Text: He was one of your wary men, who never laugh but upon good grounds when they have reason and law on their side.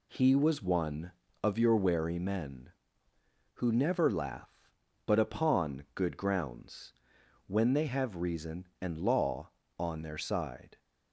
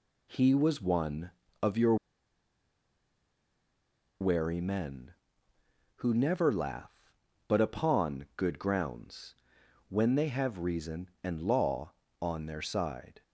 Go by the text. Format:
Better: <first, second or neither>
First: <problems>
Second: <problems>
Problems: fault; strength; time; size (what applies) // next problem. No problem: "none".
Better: first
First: pauses between "grounds" and "when"; noticeable; at 6.9 s; 0.54 s long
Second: pauses between "your" and "wary"; strong; at 1.9 s; 2.2 s long // pauses between "grounds" and "when"; noticeable; at 9.3 s; 0.54 s long